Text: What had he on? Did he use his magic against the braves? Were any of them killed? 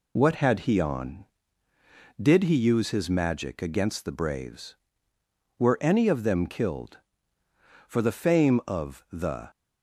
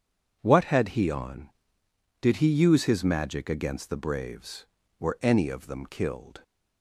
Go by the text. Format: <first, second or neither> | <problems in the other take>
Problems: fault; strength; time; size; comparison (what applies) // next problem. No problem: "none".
second | goes on to say "For the fame of the"; from 7.8 s on; 1.6 s long